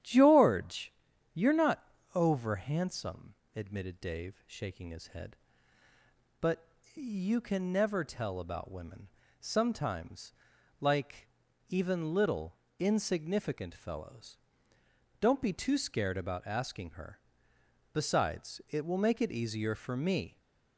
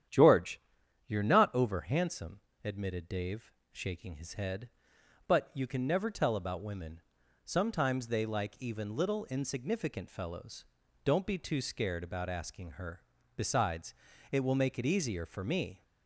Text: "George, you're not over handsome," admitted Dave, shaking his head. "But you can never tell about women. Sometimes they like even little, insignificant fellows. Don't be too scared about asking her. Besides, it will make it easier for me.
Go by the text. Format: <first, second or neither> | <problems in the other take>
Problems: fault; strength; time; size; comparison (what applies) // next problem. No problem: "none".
second | starts louder than the rest; strong; until 1.4 s; 10.5 dB; strong in the second // pauses between "not" and "over"; slight; at 1.8 s; 0.32 s long // pauses between "But" and "you"; slight; at 6.6 s; 0.28 s long // skips "they"; at 10.5 s // pauses between "like" and "even"; at 11.2 s; 0.40 s long